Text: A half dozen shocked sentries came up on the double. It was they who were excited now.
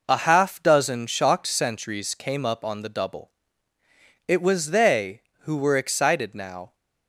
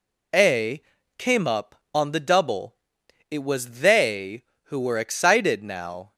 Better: first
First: none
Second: skips "half dozen shocked sentries"; at 1.0 s

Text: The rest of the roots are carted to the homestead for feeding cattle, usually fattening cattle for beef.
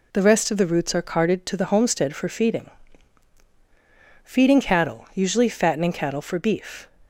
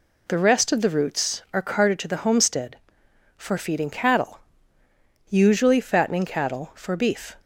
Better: second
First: says "feeding" twice; at 4.2 s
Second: none

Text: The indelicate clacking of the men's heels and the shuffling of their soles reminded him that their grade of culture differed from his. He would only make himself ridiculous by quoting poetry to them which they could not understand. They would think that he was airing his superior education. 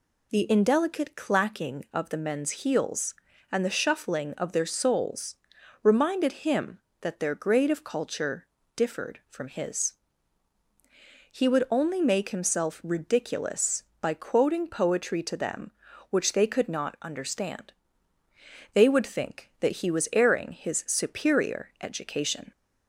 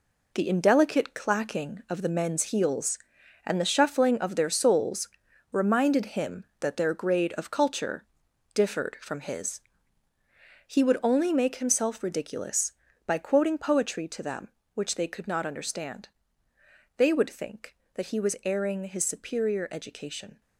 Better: first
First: pauses between "soles" and "reminded"; noticeable; at 5.3 s; 0.48 s long // pauses between "culture" and "differed"; slight; at 8.4 s; 0.28 s long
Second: gets quieter; strong; throughout; 7.5 dB // pauses between "soles" and "reminded"; at 5.0 s; 0.42 s long // pauses between "culture" and "differed"; noticeable; at 8.0 s; 0.50 s long

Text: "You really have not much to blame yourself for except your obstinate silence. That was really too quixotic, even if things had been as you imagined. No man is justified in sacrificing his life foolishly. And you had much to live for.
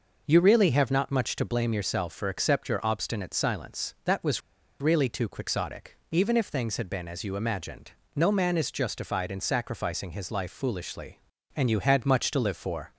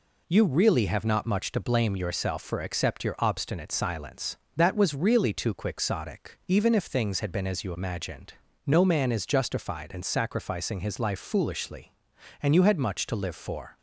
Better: second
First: pauses between "was" and "really"; at 4.4 s; 0.39 s long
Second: none

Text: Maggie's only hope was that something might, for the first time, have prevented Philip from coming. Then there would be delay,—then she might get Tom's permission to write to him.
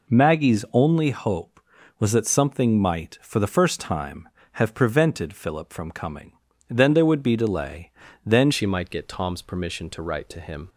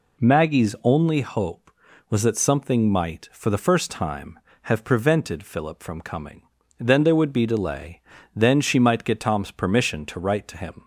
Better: second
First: changes voice at "she"; from 8.5 s on; 2.1 s long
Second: none

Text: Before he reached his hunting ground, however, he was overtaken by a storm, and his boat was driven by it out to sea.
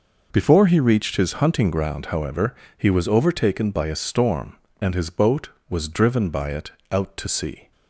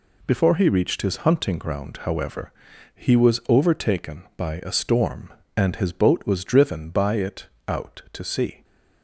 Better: neither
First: pauses between "it" and "out"; slight; at 6.7 s; 0.20 s long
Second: pauses between "it" and "out"; slight; at 7.4 s; 0.20 s long

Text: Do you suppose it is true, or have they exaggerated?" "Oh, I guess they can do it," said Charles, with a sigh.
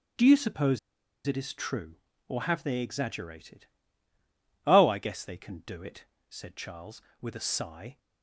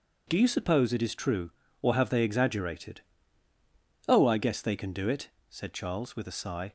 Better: second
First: starts louder than the rest; strong; until 1.6 s; 10.5 dB // pauses between "suppose" and "it"; noticeable; at 0.7 s; 0.48 s long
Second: none

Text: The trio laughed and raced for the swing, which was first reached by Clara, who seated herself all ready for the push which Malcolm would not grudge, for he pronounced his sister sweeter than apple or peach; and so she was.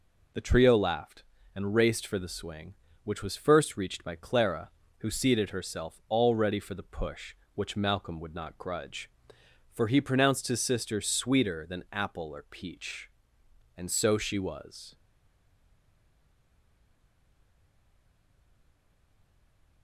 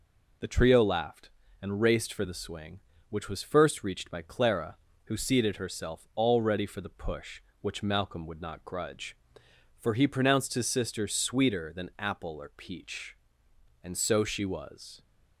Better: second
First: stays silent after the last word; strong; from 14.9 s on; 4.9 s long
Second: none

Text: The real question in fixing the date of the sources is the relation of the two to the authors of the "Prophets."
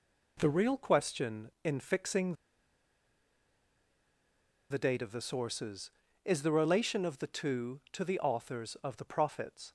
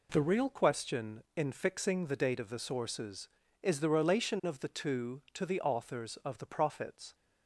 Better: second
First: pauses between "fixing" and "the"; strong; at 2.3 s; 2.3 s long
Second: none

